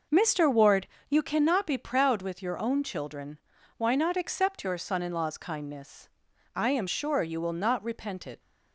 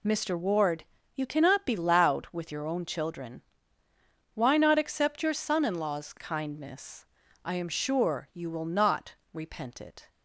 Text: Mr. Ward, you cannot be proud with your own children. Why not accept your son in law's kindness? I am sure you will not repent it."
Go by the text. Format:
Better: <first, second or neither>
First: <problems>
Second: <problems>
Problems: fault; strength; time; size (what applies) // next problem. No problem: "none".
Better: first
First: none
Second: says "loud" for "proud"; at 1.7 s // pauses between "not" and "repent"; slight; at 9.1 s; 0.18 s long